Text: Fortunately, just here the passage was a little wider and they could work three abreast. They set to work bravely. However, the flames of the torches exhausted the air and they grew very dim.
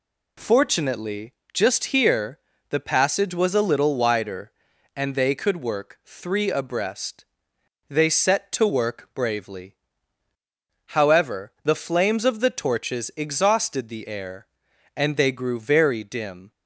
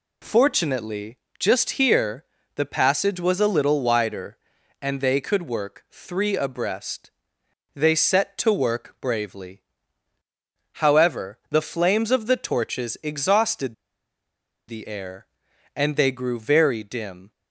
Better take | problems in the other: first | pauses between "here" and "the"; slight; at 2.2 s; 0.32 s long; slight in the first // pauses between "exhausted" and "the"; noticeable; at 13.7 s; 0.93 s long

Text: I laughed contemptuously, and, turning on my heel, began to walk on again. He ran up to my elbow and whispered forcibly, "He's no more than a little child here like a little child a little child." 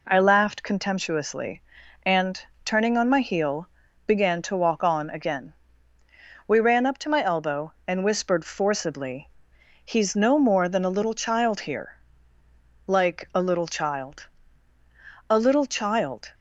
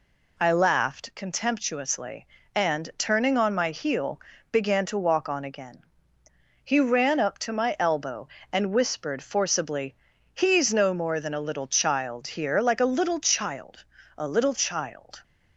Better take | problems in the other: second | says "We" for "He"; at 6.4 s // pauses between "here" and "like"; noticeable; at 11.9 s; 0.90 s long // pauses between "child" and "a"; at 14.2 s; 1.0 s long; slight in the second

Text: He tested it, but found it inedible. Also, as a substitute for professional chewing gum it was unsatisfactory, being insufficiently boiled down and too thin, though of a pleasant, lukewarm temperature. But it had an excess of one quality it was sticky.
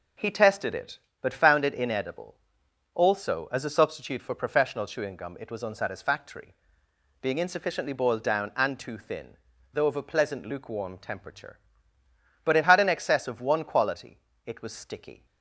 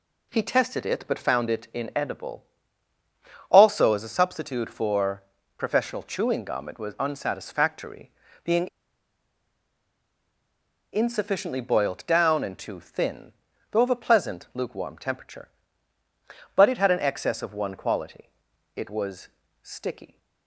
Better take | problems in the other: first | pauses between "for" and "professional"; slight; at 5.2 s; 0.34 s long // pauses between "being" and "insufficiently"; strong; at 8.6 s; 2.2 s long // pauses between "quality" and "it"; noticeable; at 18.2 s; 0.48 s long; slight in the first // pauses between "was" and "sticky"; slight; at 19.2 s; 0.34 s long

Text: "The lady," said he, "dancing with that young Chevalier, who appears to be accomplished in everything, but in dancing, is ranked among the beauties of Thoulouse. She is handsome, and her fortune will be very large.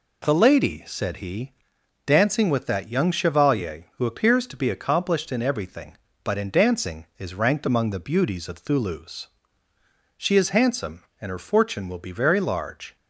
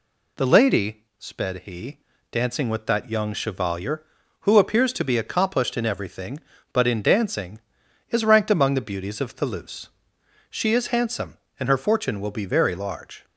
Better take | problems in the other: first | says "sped" for "said"; at 1.1 s

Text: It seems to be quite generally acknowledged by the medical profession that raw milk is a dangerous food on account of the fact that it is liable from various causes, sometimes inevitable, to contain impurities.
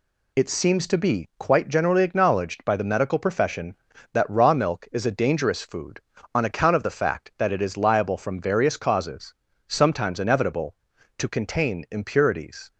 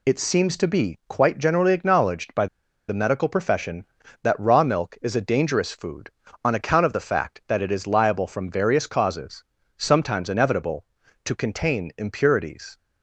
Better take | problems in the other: first | pauses between "by" and "the"; at 2.4 s; 0.42 s long

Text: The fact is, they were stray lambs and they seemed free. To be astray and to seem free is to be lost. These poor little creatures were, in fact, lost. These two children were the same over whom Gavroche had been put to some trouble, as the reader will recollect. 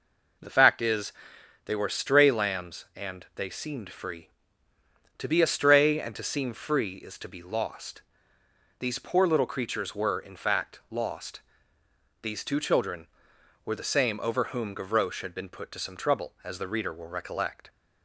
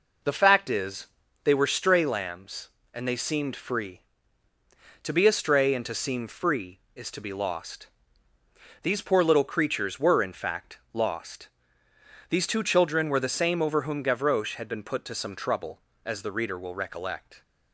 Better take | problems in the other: neither | none

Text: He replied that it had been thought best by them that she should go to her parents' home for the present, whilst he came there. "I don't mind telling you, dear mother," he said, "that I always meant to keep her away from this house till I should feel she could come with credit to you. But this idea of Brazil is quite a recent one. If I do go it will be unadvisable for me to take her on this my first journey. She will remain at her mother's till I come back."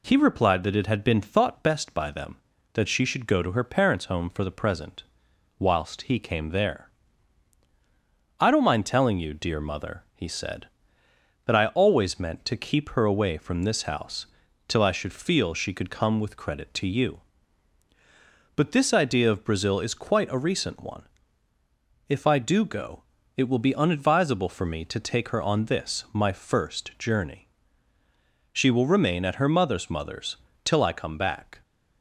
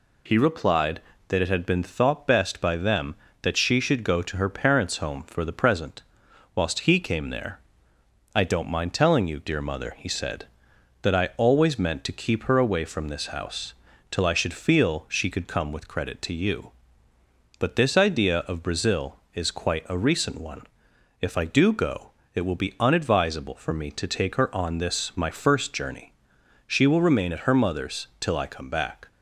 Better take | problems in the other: second | pauses between "house" and "till"; at 14.2 s; 0.40 s long; also in the second // pauses between "go" and "it"; slight; at 23.0 s; 0.36 s long; slight in the second // says "mother's" twice; at 29.8 s

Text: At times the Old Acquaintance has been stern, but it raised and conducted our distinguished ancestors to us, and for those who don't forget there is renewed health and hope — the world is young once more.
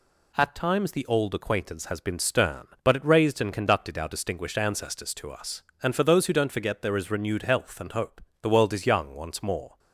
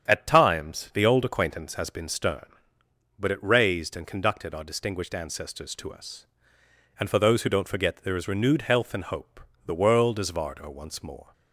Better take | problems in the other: first | starts louder than the rest; strong; until 1.1 s; 8.5 dB // says "vardo" for "young"; at 10.3 s

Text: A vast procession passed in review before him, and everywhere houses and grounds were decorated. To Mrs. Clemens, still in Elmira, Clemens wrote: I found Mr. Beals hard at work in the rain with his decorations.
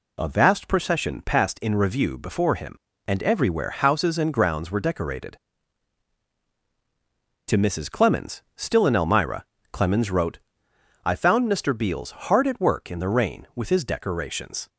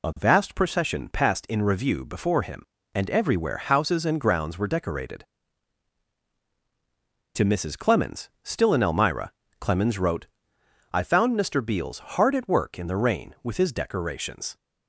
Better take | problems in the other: first | loses the start of "A"; at 0.0 s; 25 ms

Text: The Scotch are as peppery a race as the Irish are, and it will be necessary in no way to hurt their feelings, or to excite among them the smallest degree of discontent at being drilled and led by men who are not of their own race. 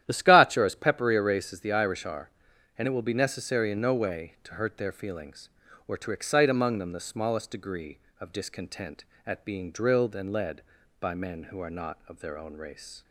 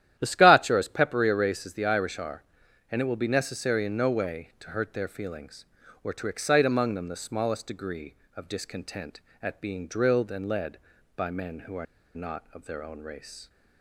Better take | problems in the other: first | starts louder than the rest; strong; until 1.2 s; 11.5 dB; strong in the first // pauses between "are" and "not"; slight; at 11.8 s; 0.29 s long

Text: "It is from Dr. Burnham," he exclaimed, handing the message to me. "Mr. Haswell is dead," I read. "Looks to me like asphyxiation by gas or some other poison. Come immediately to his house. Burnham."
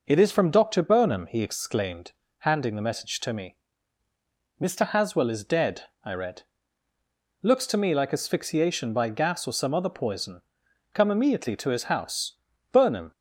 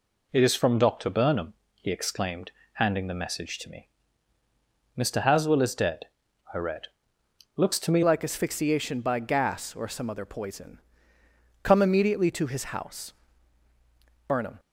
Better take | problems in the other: first | changes voice at "like"; from 8.0 s on; 6.5 s long

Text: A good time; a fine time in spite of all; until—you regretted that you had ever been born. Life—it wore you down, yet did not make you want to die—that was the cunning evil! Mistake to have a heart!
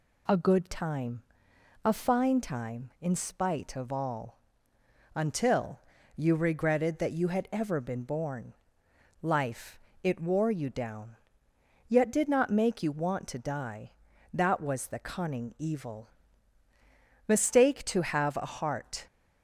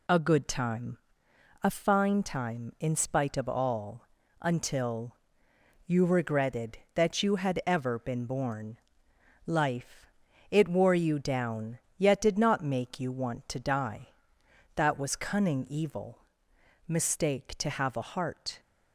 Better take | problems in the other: first | skips "the"; at 15.1 s

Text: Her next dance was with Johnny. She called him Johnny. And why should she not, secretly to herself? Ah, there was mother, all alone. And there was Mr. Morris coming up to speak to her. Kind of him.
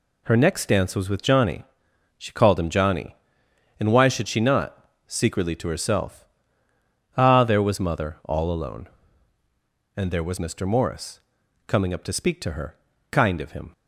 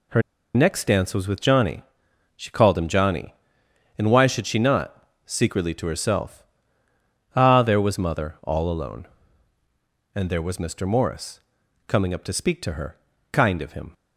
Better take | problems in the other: first | pauses between "Her" and "next"; slight; at 0.2 s; 0.33 s long // pauses between "Morris" and "coming"; noticeable; at 11.3 s; 0.48 s long; noticeable in the first

